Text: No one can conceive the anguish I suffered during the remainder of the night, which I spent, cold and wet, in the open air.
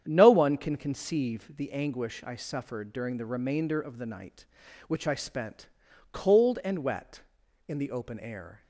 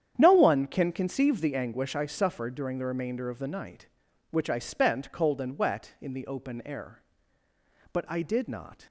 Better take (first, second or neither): first